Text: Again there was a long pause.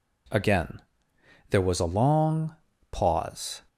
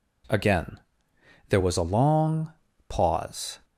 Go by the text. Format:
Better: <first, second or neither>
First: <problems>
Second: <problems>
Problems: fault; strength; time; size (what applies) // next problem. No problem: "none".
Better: neither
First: pauses between "Again" and "there"; noticeable; at 0.8 s; 0.69 s long // pauses between "long" and "pause"; slight; at 2.5 s; 0.34 s long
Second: pauses between "Again" and "there"; noticeable; at 0.7 s; 0.70 s long // pauses between "long" and "pause"; slight; at 2.5 s; 0.34 s long